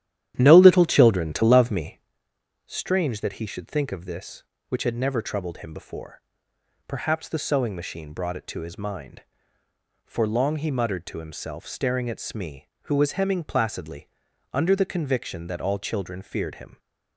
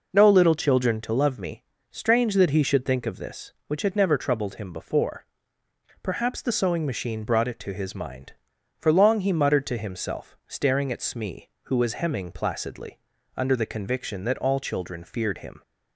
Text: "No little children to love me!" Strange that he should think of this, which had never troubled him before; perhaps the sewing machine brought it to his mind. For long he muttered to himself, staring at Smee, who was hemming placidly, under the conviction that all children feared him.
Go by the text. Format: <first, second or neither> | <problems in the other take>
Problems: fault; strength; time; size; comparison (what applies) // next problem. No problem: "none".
second | starts louder than the rest; strong; until 2.1 s; 11 dB